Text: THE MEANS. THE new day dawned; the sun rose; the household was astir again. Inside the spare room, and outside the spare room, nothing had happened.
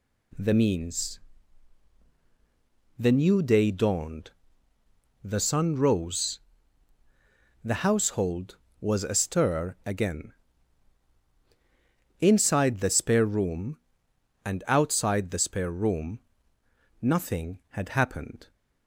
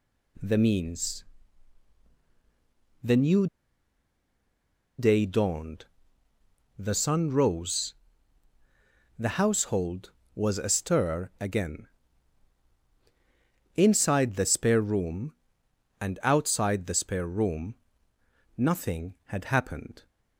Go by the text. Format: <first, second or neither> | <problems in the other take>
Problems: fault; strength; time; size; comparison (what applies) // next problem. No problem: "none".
first | pauses between "new" and "day"; strong; at 3.4 s; 1.5 s long